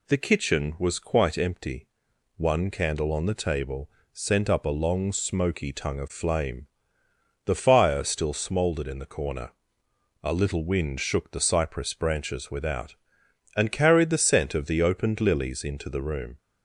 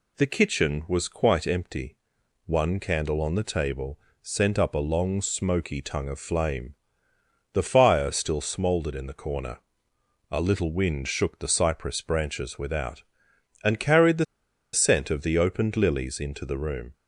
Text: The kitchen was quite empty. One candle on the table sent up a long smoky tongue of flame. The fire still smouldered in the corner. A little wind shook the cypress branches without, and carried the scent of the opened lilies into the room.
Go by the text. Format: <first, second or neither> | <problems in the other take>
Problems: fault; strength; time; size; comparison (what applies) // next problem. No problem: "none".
first | pauses between "table" and "sent"; slight; at 3.9 s; 0.24 s long; slight in the first // pauses between "the" and "scent"; noticeable; at 14.2 s; 0.48 s long